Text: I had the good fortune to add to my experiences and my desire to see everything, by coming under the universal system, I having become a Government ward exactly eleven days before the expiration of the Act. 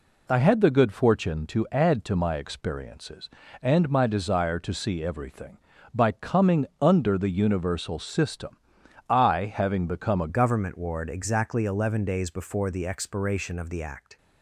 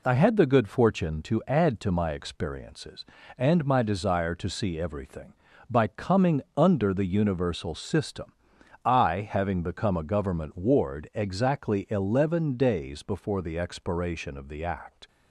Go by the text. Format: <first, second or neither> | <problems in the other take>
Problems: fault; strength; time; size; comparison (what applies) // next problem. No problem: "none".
second | pauses between "coming" and "under"; slight; at 6.6 s; 0.16 s long; slight in the second // changes voice at "Government"; from 10.2 s on; 3.9 s long